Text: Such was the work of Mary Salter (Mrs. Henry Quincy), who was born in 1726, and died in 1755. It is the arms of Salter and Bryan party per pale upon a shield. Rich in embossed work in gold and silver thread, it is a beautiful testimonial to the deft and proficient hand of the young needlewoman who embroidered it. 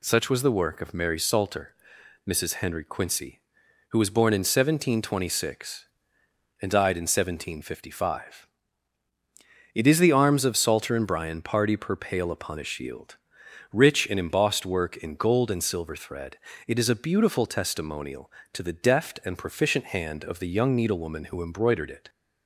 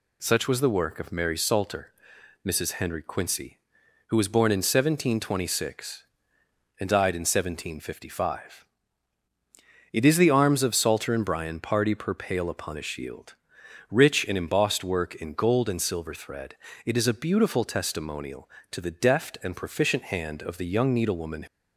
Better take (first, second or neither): first